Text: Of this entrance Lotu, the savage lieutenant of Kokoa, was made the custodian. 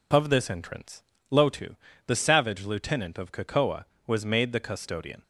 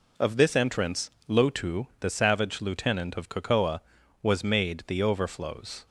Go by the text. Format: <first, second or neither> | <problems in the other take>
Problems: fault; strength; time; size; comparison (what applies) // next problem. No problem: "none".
first | pauses between "entrance" and "Lotu"; slight; at 1.0 s; 0.18 s long; slight in the first // says "overflows" for "custodian"; at 5.0 s